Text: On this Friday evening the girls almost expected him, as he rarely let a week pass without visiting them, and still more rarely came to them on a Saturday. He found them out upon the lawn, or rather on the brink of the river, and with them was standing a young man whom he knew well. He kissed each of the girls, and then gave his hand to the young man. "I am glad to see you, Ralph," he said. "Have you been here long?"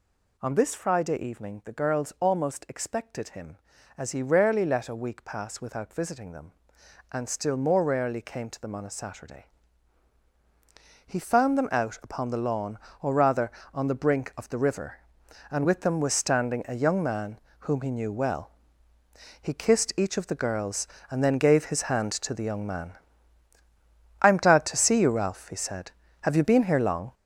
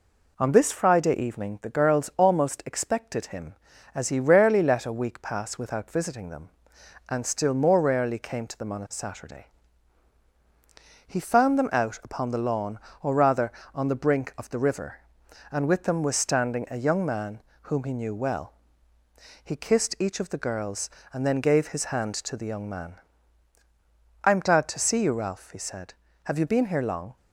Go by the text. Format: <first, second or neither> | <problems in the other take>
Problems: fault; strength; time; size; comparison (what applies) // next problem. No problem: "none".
second | gets louder; strong; throughout; 7 dB // pauses between "man" and "whom"; slight; at 17.3 s; 0.20 s long; slight in the second